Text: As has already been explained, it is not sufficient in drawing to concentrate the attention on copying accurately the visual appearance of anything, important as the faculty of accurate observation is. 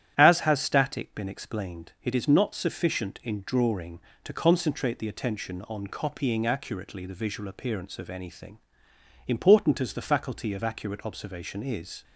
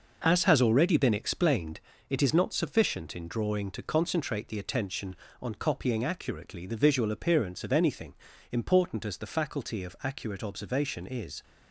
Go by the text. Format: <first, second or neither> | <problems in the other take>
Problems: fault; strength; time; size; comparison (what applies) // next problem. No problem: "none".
second | starts louder than the rest; strong; until 1.1 s; 11 dB // says "static" for "already"; at 0.6 s